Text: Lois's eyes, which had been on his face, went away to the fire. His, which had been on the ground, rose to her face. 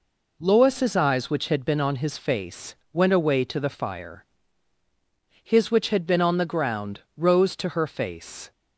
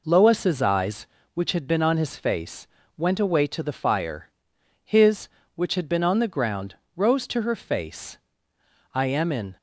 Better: first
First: none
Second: goes on to say "I am in"; noticeable; from 8.9 s on; 0.64 s long

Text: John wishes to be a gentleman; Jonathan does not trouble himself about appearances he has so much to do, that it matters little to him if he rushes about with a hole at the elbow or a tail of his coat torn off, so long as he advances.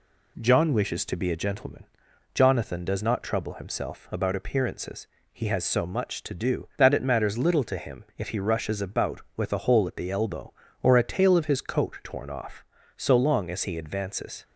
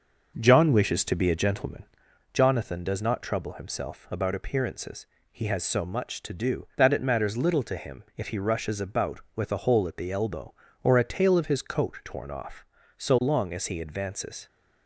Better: first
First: pauses between "appearances" and "he"; slight; at 5.0 s; 0.24 s long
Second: starts louder than the rest; noticeable; until 2.1 s; 6 dB // pauses between "appearances" and "he"; slight; at 5.0 s; 0.24 s long

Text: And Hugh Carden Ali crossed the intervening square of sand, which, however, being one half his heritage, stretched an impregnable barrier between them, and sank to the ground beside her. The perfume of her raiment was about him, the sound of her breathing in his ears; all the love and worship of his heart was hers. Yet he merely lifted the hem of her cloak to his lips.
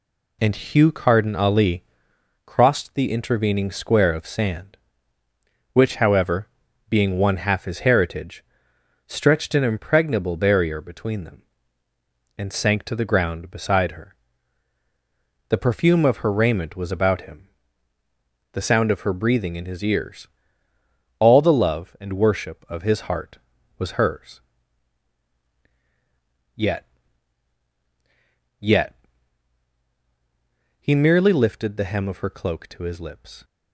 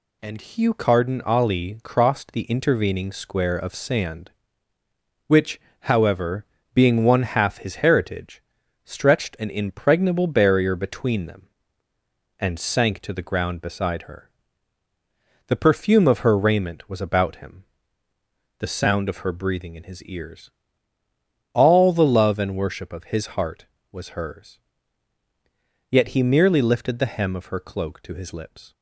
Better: second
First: pauses between "Ali" and "crossed"; noticeable; at 1.8 s; 0.62 s long // says "Yet" twice; at 28.6 s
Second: none

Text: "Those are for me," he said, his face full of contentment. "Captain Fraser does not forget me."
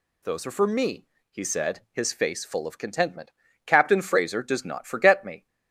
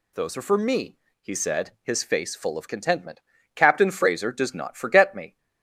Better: neither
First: none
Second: none

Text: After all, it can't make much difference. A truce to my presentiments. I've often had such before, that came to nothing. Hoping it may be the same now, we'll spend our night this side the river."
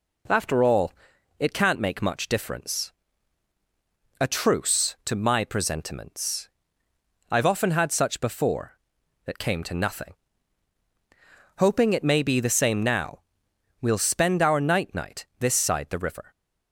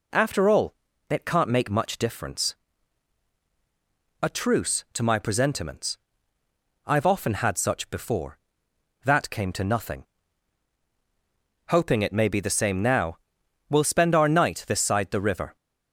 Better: second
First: says "night" twice; at 14.9 s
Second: none

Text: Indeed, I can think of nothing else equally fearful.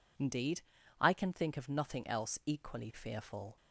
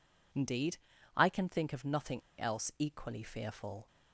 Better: first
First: none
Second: pauses between "nothing" and "else"; slight; at 2.2 s; 0.19 s long

